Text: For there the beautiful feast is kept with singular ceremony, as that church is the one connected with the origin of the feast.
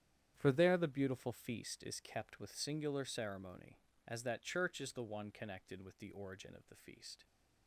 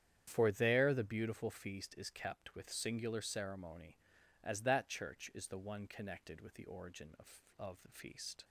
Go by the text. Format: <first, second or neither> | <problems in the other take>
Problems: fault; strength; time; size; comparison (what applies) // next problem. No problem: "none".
first | starts louder than the rest; strong; until 1.2 s; 9.5 dB; strong in the first // says "of" twice; at 7.5 s